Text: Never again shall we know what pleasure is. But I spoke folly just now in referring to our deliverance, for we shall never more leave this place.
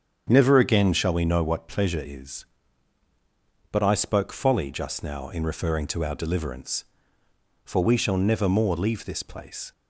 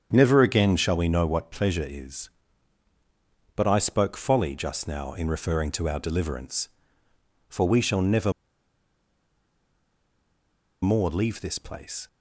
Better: first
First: starts louder than the rest; strong; until 1.3 s; 7.5 dB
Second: starts louder than the rest; strong; until 1.1 s; 8 dB // pauses between "never" and "more"; strong; at 8.3 s; 2.5 s long

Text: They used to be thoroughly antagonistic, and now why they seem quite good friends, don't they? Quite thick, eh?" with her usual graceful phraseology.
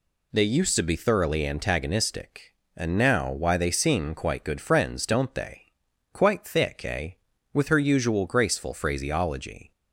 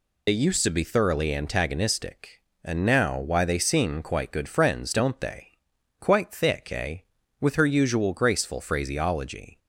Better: first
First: none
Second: loses the start of "They"; at 0.2 s; 75 ms

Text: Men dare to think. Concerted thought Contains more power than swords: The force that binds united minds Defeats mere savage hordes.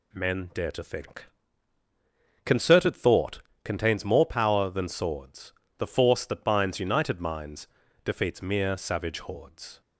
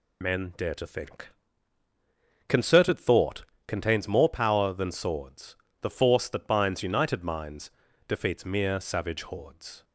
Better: first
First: pauses between "thought" and "Contains"; slight; at 3.4 s; 0.22 s long // pauses between "minds" and "Defeats"; slight; at 7.6 s; 0.34 s long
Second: loses the start of "Men"; at 0.2 s; 50 ms // pauses between "thought" and "Contains"; slight; at 3.4 s; 0.22 s long // pauses between "minds" and "Defeats"; slight; at 7.7 s; 0.34 s long

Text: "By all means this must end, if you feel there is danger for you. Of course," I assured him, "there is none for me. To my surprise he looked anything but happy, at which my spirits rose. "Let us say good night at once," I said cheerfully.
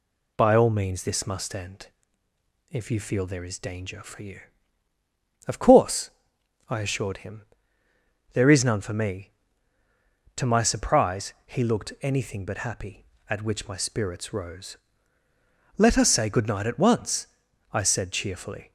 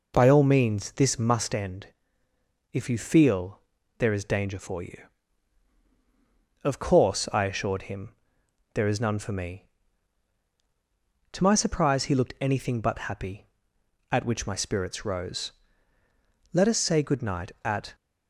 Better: first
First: none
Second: pauses between "feel" and "there"; at 3.5 s; 0.40 s long // stops before "once I said cheerfully"; at 17.9 s

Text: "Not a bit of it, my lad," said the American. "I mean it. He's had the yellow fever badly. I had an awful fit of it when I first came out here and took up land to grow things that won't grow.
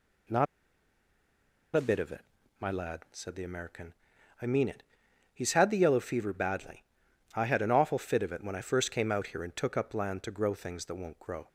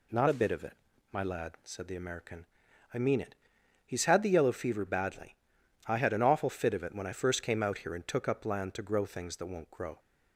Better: second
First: pauses between "Not" and "a"; strong; at 0.4 s; 1.2 s long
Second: none

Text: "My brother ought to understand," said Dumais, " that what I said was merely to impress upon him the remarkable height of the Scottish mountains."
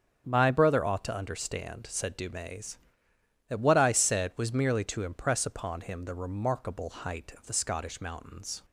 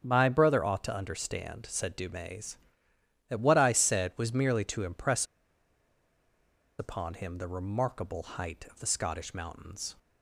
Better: first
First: none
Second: pauses between "impress" and "upon"; strong; at 5.2 s; 1.5 s long

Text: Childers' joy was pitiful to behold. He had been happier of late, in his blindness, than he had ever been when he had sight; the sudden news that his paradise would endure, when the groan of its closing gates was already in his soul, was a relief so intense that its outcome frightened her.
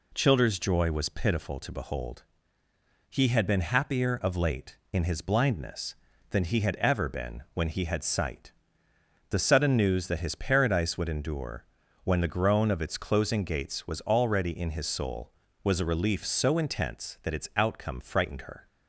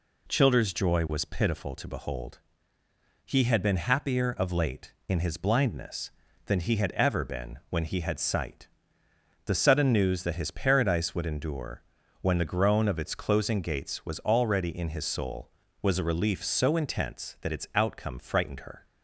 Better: neither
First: none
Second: none

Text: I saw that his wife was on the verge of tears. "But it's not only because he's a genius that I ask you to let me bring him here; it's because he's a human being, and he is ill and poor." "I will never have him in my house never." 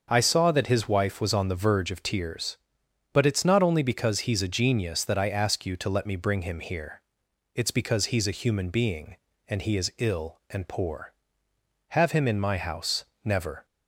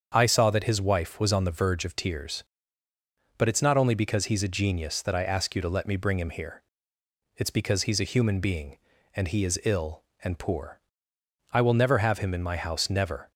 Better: second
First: starts louder than the rest; until 1.1 s; 6.5 dB // skips "I will never"; at 11.5 s // pauses between "house" and "never"; slight; at 13.0 s; 0.18 s long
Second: starts louder than the rest; until 1.1 s; 7 dB

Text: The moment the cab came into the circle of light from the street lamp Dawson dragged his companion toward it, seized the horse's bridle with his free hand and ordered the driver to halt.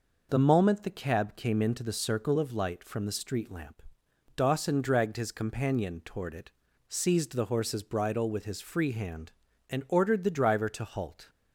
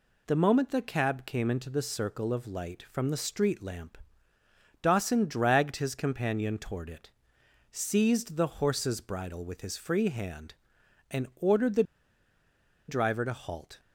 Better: first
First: pauses between "lamp" and "Dawson"; noticeable; at 3.8 s; 0.54 s long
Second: pauses between "lamp" and "Dawson"; noticeable; at 3.9 s; 0.84 s long // pauses between "the" and "driver"; at 11.8 s; 1.0 s long

